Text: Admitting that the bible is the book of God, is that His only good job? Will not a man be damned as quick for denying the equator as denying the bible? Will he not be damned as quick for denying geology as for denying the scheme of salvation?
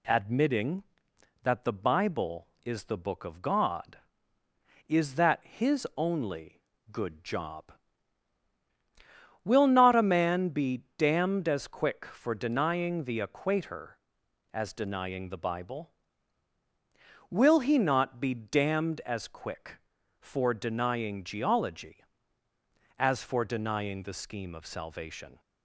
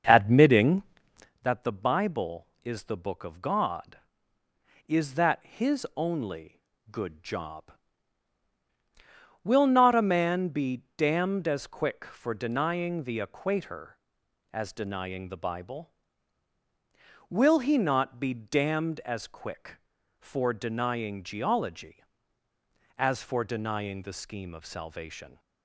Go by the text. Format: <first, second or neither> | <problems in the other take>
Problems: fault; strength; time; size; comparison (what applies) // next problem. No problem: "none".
first | starts louder than the rest; until 1.4 s; 6.5 dB // pauses between "only" and "good"; slight; at 6.5 s; 0.32 s long; slight in the first // pauses between "be" and "damned"; slight; at 10.8 s; 0.16 s long; slight in the first